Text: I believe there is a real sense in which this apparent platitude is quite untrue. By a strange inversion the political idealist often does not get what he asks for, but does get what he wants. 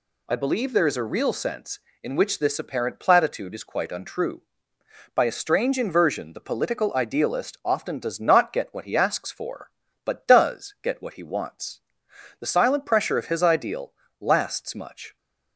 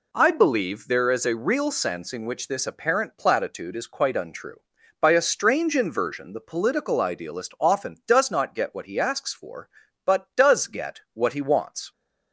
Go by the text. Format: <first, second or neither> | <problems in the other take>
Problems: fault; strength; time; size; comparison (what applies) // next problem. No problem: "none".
second | goes on to say "The silent pressure of his ideal lasts much"; strong; from 12.4 s on; 2.7 s long